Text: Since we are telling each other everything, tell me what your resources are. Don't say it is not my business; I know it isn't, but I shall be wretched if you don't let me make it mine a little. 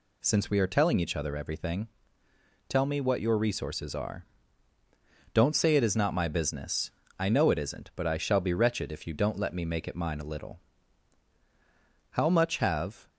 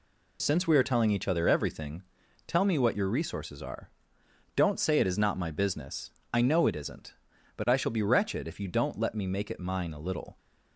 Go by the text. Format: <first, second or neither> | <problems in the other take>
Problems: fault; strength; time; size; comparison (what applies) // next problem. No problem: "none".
second | goes on to say "How much have"; noticeable; from 12.1 s on; 0.98 s long